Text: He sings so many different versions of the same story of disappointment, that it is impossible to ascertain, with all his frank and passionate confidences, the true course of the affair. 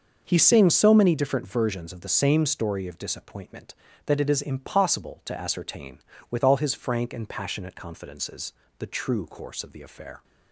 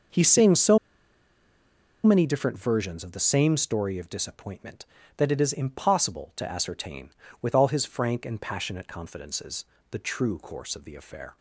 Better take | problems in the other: first | starts louder than the rest; until 2.3 s; 6.5 dB; also in the first // pauses between "so" and "many"; strong; at 0.7 s; 1.2 s long

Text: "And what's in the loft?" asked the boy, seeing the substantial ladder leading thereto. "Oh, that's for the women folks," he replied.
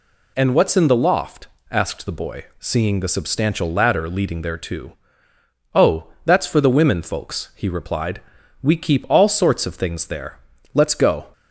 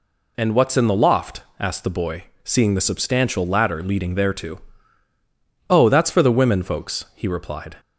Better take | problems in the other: second | goes on to say "We keep all sorts of things there Let's go"; strong; from 8.6 s on; 2.6 s long

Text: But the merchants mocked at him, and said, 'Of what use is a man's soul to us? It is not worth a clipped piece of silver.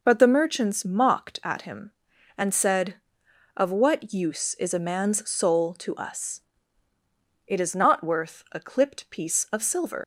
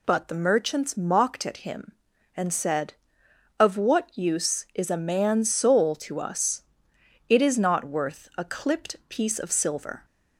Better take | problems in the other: second | leaves "silver" unfinished; at 10.0 s; 105 ms

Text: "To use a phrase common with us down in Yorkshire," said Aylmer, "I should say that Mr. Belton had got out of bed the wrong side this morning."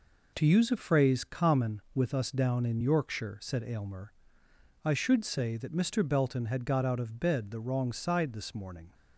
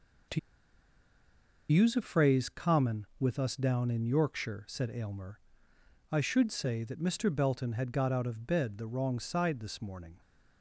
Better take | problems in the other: first | pauses between "To" and "use"; strong; at 0.3 s; 1.3 s long

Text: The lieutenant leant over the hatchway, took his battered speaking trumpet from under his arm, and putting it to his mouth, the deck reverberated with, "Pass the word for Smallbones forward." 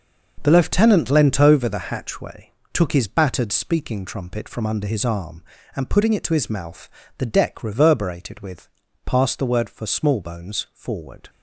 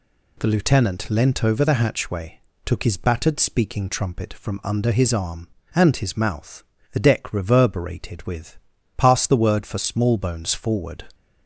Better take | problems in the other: first | skips "putting it to"; at 5.9 s

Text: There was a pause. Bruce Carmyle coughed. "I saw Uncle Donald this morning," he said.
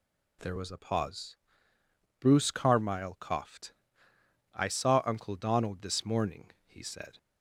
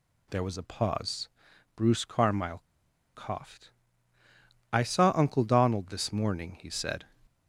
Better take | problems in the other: first | pauses between "Carmyle" and "coughed"; noticeable; at 2.6 s; 0.51 s long

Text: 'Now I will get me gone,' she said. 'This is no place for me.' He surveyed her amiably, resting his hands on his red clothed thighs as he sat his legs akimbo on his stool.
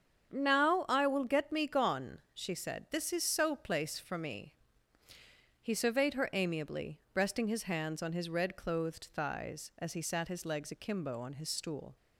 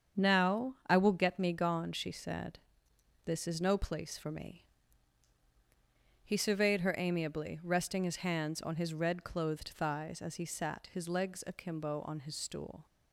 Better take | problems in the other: second | starts louder than the rest; strong; until 1.3 s; 7.5 dB; strong in the second // says "so" for "no"; at 3.2 s

